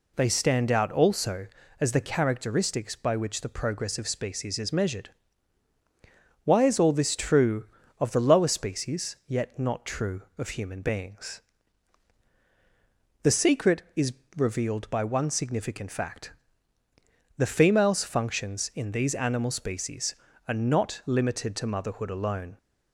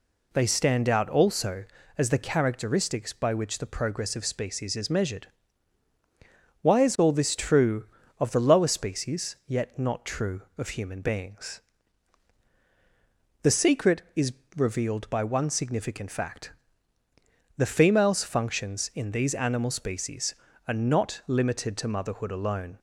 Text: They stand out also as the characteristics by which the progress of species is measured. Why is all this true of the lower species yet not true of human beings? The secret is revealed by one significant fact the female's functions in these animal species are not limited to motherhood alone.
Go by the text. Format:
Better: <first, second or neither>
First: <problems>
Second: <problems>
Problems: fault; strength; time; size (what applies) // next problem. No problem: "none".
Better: neither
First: pauses between "is" and "revealed"; slight; at 14.1 s; 0.24 s long // pauses between "fact" and "the"; at 16.3 s; 1.0 s long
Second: pauses between "is" and "revealed"; slight; at 14.3 s; 0.24 s long // pauses between "fact" and "the"; at 16.5 s; 1.0 s long